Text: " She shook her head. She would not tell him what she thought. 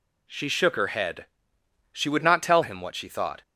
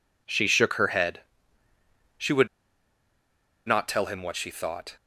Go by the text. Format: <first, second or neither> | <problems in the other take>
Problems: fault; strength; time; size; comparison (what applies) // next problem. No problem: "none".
first | pauses between "would" and "not"; at 2.4 s; 1.2 s long